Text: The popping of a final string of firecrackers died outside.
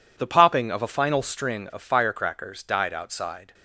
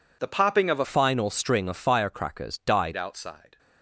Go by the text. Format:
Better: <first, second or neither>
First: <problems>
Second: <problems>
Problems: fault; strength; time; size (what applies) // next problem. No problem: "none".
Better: first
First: none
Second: changes voice from "final" to "died"; from 0.8 to 2.9 s; 2.1 s long